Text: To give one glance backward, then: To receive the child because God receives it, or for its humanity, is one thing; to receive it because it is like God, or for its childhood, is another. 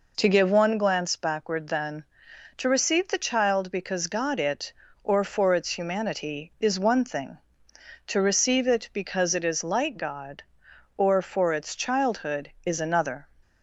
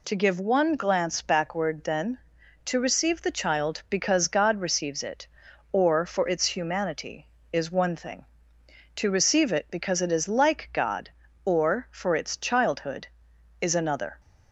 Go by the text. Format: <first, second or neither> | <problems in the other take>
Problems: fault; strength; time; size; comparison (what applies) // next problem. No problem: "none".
second | skips "receives"; at 4.3 s